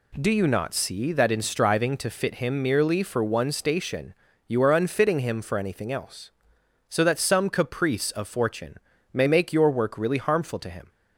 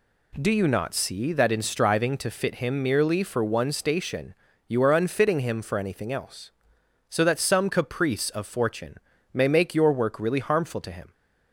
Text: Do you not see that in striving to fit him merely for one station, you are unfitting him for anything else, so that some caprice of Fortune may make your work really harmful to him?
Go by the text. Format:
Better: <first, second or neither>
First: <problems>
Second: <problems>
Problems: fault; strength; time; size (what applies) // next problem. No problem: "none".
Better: neither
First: pauses between "Fortune" and "may"; at 8.7 s; 0.38 s long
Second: pauses between "Fortune" and "may"; at 8.9 s; 0.38 s long